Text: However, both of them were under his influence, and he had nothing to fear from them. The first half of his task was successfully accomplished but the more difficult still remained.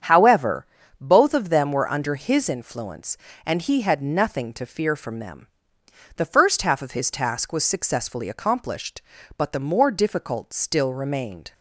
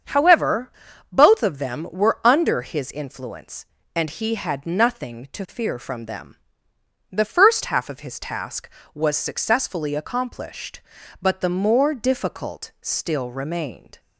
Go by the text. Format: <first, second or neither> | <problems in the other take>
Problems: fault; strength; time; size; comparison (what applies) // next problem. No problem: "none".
neither | starts louder than the rest; strong; the same in both